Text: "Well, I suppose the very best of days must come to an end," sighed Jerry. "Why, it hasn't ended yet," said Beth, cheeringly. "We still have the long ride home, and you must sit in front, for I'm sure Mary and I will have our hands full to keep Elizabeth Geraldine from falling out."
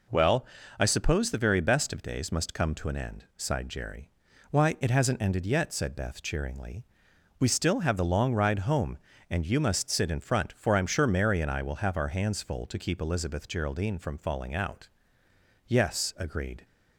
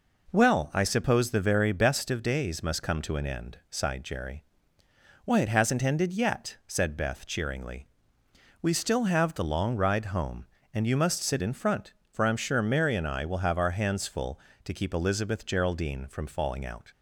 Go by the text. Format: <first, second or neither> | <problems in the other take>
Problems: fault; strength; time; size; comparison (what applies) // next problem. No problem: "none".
second | goes on to say "Yes agreed"; noticeable; from 15.6 s on; 0.98 s long